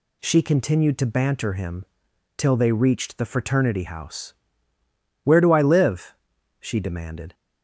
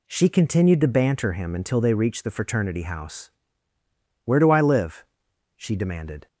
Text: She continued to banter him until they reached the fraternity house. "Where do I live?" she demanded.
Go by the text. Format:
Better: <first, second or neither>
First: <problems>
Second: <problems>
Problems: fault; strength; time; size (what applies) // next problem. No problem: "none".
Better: second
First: says "till" for "until"; at 2.3 s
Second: none